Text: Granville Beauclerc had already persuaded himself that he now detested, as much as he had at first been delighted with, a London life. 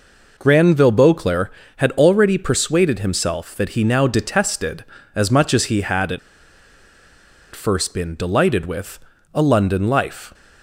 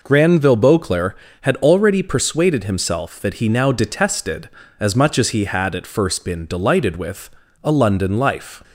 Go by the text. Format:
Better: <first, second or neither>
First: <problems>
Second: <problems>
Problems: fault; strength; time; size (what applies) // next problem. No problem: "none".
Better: second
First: pauses between "at" and "first"; strong; at 6.1 s; 1.3 s long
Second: none